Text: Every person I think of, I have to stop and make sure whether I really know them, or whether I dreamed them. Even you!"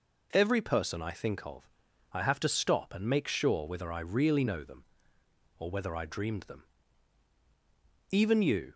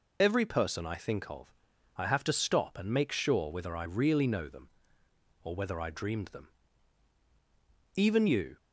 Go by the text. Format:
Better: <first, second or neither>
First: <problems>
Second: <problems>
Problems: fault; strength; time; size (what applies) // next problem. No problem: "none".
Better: first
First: none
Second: loses the start of "Every"; at 0.2 s; 55 ms